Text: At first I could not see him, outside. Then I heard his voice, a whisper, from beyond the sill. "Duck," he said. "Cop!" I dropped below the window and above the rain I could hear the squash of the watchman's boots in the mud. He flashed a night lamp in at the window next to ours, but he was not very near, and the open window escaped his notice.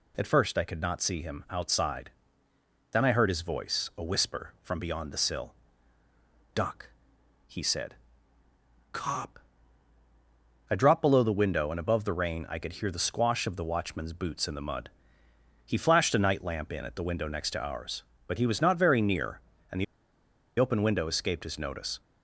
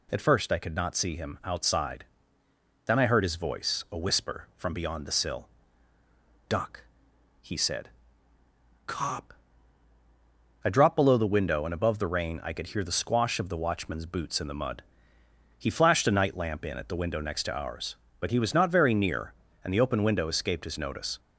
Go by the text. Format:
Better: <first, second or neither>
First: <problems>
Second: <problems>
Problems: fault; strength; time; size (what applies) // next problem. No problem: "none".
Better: second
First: pauses between "the" and "open"; noticeable; at 19.8 s; 0.74 s long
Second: none